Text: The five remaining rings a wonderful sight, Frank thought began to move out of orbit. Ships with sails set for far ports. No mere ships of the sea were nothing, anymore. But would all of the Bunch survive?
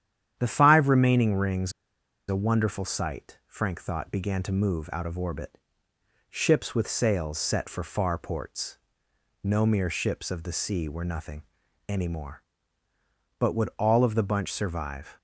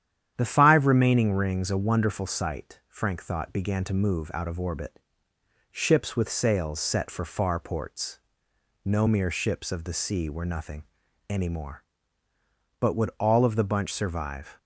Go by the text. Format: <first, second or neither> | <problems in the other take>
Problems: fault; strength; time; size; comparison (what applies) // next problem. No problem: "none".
second | starts louder than the rest; strong; until 1.4 s; 10 dB; strong in the second // pauses between "rings" and "a"; noticeable; at 1.7 s; 0.57 s long